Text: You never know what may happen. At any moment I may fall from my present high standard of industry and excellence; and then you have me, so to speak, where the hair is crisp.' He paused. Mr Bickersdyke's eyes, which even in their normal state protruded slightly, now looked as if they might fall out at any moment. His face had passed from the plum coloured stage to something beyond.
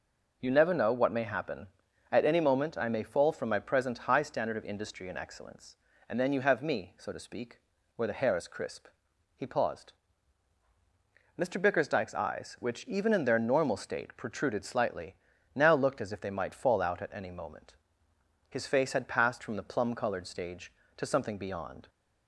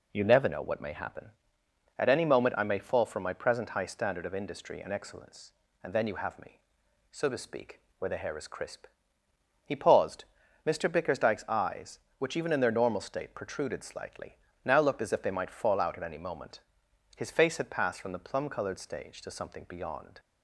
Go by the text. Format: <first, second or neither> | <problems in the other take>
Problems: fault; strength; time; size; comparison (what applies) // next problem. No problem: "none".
neither | none